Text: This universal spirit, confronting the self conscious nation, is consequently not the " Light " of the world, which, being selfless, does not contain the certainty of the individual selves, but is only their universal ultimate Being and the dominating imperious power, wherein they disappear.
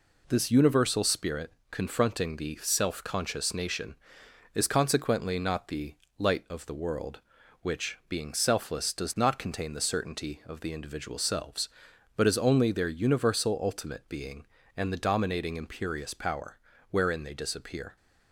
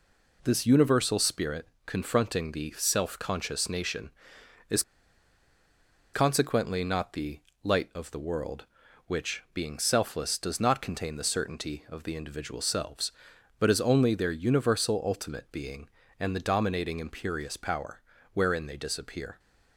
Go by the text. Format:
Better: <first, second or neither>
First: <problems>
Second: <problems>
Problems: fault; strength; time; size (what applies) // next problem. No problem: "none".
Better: first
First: none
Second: pauses between "is" and "consequently"; strong; at 4.8 s; 1.3 s long